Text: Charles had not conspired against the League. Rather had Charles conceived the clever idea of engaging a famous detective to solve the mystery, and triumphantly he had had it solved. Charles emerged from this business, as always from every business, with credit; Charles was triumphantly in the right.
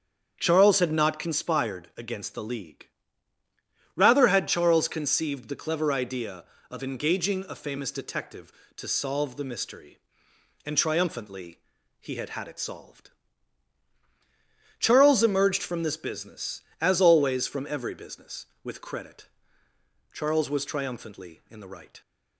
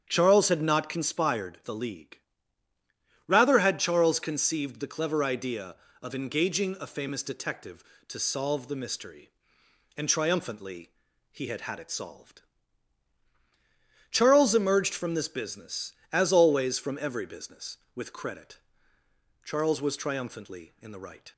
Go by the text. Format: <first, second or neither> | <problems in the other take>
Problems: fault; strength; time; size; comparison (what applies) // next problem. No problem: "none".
first | starts louder than the rest; strong; until 1.0 s; 8 dB; strong in the first // skips "against"; at 1.6 s // pauses between "triumphantly" and "he"; at 10.9 s; 0.40 s long; also in the first